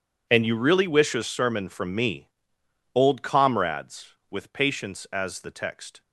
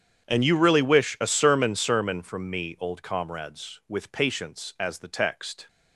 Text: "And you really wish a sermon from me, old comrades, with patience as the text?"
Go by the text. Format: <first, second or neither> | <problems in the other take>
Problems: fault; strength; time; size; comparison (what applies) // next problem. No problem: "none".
first | starts louder than the rest; strong; until 1.2 s; 8 dB // says "sermon" twice; at 1.7 s